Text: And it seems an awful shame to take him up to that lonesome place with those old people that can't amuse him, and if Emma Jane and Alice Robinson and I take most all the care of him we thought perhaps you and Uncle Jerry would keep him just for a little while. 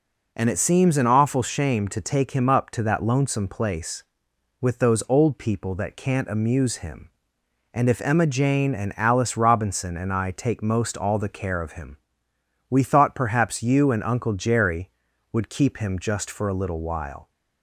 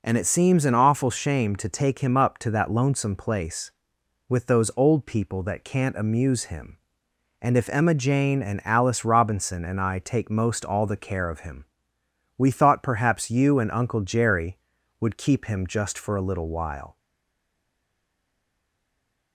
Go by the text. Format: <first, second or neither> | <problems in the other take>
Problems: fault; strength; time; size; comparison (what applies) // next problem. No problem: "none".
first | pauses between "him" and "we"; noticeable; at 11.6 s; 0.72 s long; noticeable in the first // stays silent after the last word; from 16.9 s on; 2.4 s long